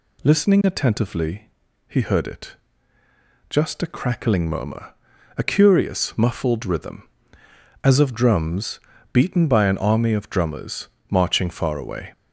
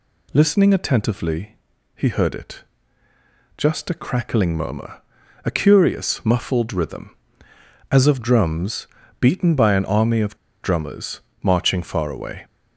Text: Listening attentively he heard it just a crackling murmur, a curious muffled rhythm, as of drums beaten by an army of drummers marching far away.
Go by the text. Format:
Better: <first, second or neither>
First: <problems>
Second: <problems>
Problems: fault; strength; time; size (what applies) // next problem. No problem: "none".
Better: first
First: pauses between "attentively" and "he"; at 1.4 s; 0.40 s long // pauses between "it" and "just"; noticeable; at 2.5 s; 0.96 s long // pauses between "drums" and "beaten"; slight; at 8.8 s; 0.32 s long // pauses between "drummers" and "marching"; slight; at 10.8 s; 0.22 s long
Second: pauses between "attentively" and "he"; at 1.5 s; 0.40 s long // pauses between "it" and "just"; noticeable; at 2.6 s; 0.96 s long // pauses between "drums" and "beaten"; slight; at 8.8 s; 0.32 s long // pauses between "of" and "drummers"; slight; at 10.3 s; 0.25 s long // pauses between "drummers" and "marching"; slight; at 11.2 s; 0.22 s long